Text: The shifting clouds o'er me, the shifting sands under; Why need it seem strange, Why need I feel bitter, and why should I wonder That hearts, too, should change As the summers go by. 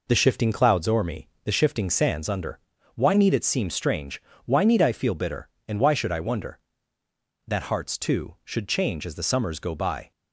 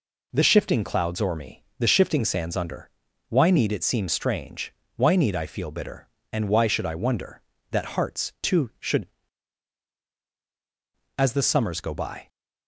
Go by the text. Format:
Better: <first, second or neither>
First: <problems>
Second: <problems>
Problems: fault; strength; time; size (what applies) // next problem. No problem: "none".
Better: first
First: none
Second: skips "change"; at 10.1 s